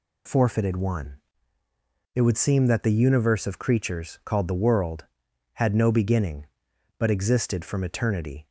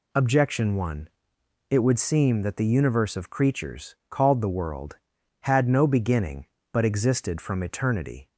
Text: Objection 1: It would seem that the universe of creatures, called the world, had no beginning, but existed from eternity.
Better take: second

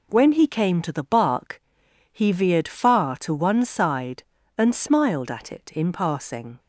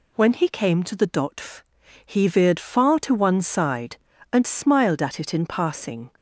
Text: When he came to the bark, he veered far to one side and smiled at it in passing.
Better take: first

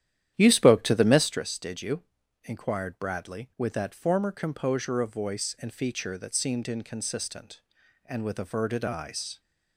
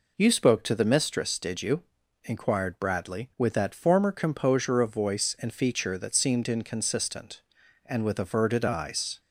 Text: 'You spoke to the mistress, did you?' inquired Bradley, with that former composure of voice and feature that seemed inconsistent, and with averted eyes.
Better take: second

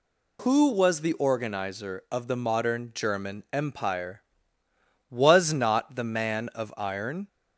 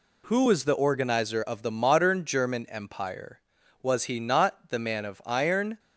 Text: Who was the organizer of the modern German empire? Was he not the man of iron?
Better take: second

